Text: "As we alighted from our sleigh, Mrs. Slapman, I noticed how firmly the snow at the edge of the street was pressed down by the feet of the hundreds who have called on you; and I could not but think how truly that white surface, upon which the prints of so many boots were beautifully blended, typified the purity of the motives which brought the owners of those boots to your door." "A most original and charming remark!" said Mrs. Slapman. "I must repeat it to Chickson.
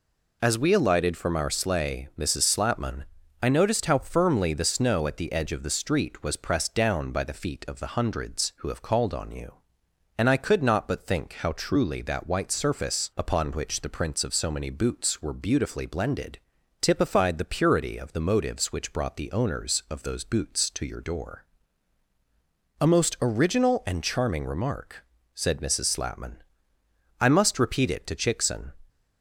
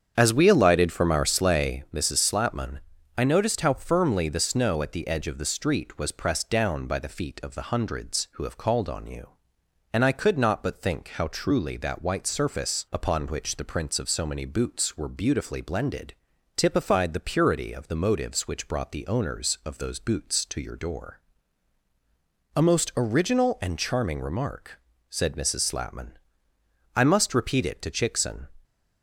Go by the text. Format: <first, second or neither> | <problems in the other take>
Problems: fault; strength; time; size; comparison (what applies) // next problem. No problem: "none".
first | starts louder than the rest; strong; until 2.0 s; 8 dB